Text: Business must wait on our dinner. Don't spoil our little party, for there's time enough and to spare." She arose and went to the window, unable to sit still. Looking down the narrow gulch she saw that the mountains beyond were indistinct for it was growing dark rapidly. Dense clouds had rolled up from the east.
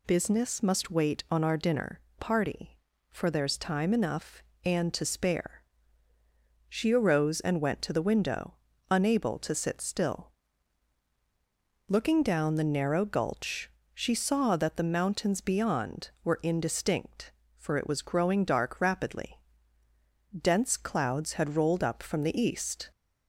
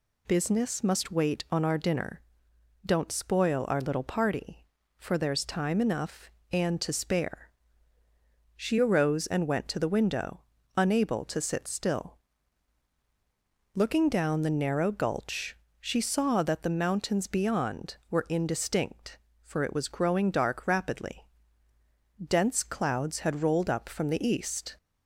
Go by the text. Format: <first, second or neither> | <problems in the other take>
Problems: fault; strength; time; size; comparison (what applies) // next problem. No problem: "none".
second | skips "Don't spoil our little"; at 2.0 s // pauses between "gulch" and "she"; slight; at 13.7 s; 0.20 s long; slight in the second